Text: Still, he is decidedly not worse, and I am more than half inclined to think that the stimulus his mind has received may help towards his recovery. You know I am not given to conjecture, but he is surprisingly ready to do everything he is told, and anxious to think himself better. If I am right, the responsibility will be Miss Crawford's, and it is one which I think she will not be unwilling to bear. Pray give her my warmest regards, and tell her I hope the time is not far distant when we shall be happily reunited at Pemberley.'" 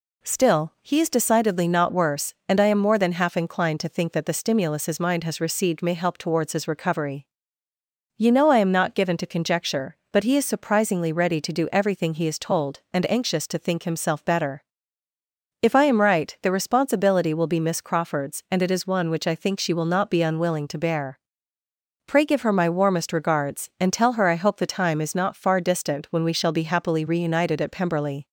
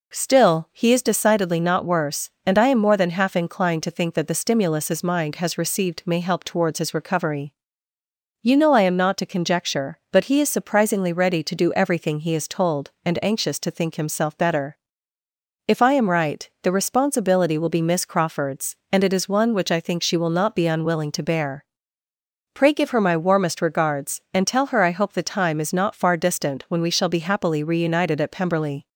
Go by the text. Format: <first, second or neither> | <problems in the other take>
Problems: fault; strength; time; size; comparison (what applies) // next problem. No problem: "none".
first | skips "given"; at 9.1 s